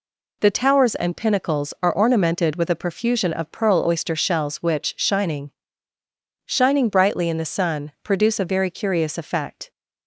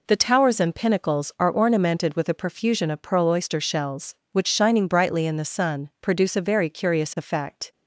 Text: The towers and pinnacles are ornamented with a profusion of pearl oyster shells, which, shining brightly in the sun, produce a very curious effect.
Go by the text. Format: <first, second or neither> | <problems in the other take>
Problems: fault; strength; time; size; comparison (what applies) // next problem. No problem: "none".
second | says "shining" twice; at 6.4 s